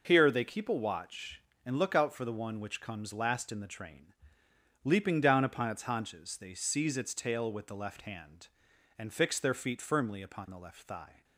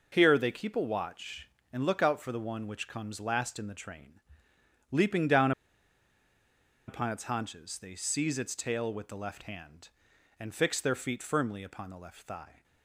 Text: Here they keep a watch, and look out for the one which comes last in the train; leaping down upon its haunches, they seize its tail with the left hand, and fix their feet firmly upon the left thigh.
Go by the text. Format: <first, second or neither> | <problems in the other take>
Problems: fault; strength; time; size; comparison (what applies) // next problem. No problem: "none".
first | pauses between "down" and "upon"; strong; at 5.5 s; 1.3 s long